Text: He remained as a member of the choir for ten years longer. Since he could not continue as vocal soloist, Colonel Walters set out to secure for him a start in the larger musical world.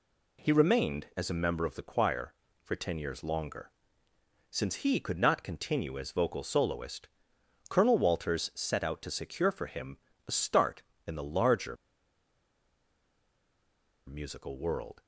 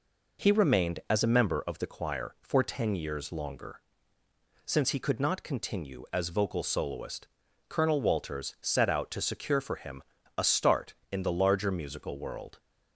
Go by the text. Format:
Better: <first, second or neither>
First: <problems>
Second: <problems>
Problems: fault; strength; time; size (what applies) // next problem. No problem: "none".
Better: second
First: pauses between "him" and "a"; slight; at 9.9 s; 0.28 s long // pauses between "larger" and "musical"; strong; at 11.7 s; 2.3 s long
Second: pauses between "him" and "a"; slight; at 10.0 s; 0.34 s long